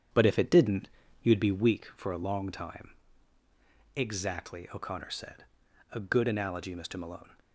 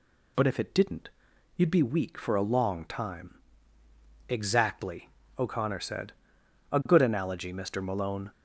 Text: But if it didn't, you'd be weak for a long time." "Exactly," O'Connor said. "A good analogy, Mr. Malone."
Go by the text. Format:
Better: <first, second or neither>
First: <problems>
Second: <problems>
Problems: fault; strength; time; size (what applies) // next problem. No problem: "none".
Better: second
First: starts louder than the rest; strong; until 1.9 s; 8 dB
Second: none